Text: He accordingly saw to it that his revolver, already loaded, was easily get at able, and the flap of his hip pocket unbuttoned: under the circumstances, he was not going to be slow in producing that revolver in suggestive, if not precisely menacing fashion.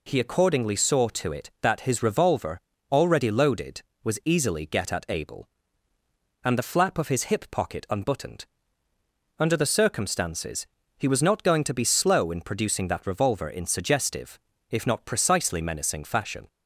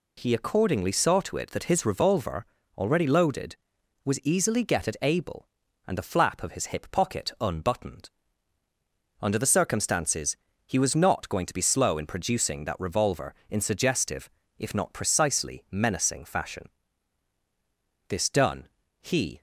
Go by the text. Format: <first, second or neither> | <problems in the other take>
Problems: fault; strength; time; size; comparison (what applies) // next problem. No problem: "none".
first | goes on to say "This done he"; from 18.0 s on; 1.3 s long